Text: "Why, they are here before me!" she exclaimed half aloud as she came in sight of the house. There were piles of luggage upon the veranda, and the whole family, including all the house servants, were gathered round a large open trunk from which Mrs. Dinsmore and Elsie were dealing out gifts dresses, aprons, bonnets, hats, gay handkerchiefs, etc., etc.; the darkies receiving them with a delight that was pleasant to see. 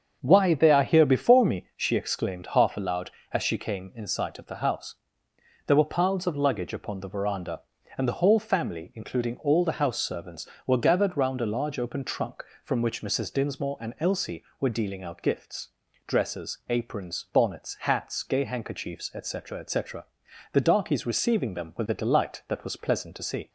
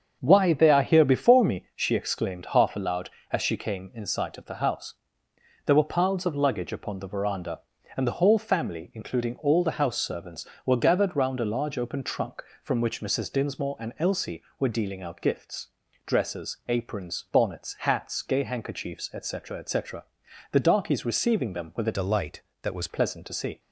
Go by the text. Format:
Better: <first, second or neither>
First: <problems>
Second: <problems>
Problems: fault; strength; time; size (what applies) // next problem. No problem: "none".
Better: first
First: starts louder than the rest; until 1.2 s; 7 dB // pauses between "gifts" and "dresses"; slight; at 15.6 s; 0.36 s long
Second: starts louder than the rest; until 1.2 s; 7 dB // pauses between "gifts" and "dresses"; slight; at 15.6 s; 0.36 s long // changes voice from "delight" to "was"; from 21.9 to 22.8 s; 0.9 s long